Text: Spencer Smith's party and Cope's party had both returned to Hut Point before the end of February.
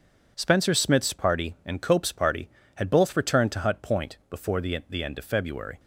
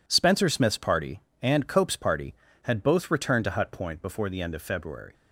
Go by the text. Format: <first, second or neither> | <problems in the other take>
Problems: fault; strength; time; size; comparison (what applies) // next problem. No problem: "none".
second | says "the" twice; at 4.8 s